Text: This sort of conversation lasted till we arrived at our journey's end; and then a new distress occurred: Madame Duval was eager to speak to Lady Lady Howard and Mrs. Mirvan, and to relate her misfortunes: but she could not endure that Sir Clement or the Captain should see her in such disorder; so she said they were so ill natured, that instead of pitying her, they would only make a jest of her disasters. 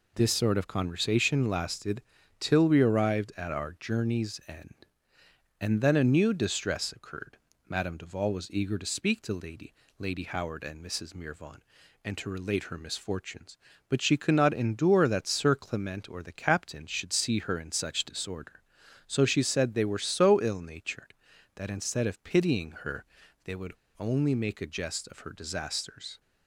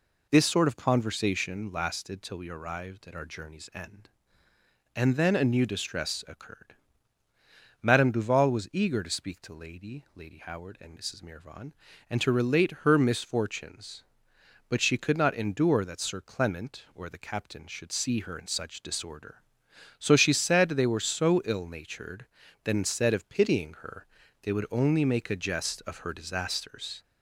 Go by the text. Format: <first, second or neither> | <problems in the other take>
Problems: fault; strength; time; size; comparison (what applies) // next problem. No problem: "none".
second | pauses between "lasted" and "till"; at 2.0 s; 0.40 s long // pauses between "Lady" and "Lady"; slight; at 9.7 s; 0.26 s long // pauses between "would" and "only"; slight; at 23.7 s; 0.26 s long